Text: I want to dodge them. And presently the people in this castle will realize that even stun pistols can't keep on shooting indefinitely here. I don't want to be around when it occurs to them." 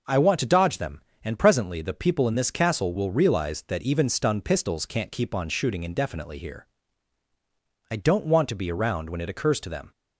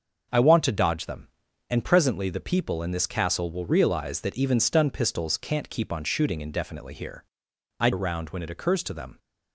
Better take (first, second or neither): first